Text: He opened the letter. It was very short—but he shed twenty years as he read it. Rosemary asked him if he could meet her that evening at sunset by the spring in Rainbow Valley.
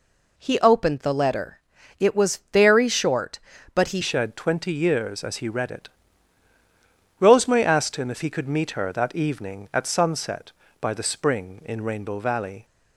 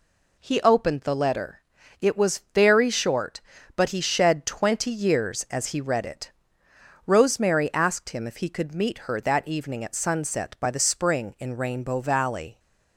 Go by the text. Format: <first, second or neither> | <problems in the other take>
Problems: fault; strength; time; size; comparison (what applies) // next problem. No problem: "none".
second | changes voice at "shed"; from 4.0 s on; 8.6 s long